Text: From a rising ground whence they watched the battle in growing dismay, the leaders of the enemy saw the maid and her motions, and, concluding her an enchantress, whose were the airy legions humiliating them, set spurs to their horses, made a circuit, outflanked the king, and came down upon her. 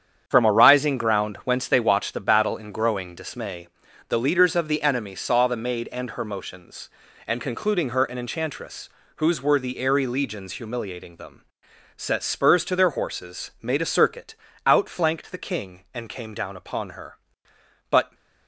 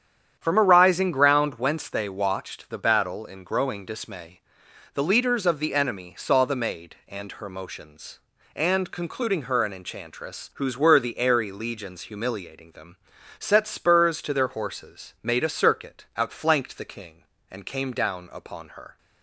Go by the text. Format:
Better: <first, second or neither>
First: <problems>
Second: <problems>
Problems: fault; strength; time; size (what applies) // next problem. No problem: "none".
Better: second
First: starts louder than the rest; strong; until 1.2 s; 8.5 dB // goes on to say "But"; slight; from 17.8 s on; 0.24 s long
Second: starts louder than the rest; strong; until 1.4 s; 9 dB